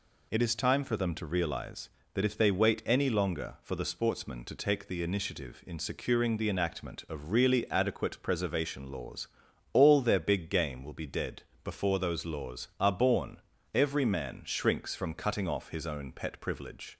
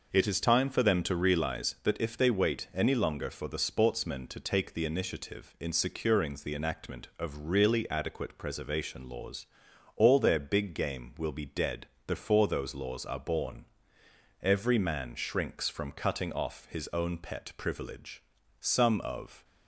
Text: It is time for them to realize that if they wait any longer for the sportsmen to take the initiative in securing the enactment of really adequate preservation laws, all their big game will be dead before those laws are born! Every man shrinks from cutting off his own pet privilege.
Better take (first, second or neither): first